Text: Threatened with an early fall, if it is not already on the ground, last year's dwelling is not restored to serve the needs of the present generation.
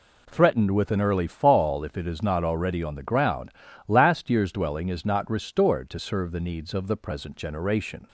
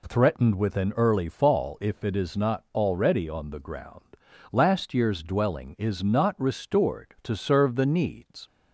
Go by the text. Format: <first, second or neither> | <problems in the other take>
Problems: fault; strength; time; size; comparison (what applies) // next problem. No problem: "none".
first | stops before "of the present generation"; at 8.4 s